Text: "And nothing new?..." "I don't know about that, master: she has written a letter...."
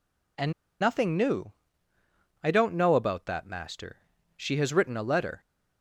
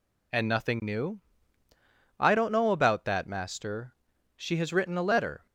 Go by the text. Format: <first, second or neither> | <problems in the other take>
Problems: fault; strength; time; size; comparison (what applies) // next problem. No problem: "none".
second | pauses between "And" and "nothing"; slight; at 0.5 s; 0.30 s long